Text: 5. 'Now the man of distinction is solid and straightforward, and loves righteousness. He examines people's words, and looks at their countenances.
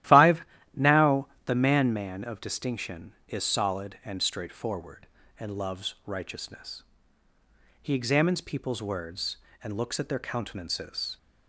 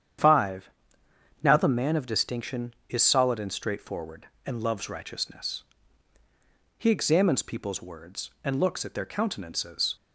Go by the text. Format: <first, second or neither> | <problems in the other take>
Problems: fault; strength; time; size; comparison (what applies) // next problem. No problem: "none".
second | starts louder than the rest; strong; until 1.5 s; 13.5 dB; strong in the second // pauses between "Now" and "the"; slight; at 1.2 s; 0.16 s long // says "man" twice; at 1.9 s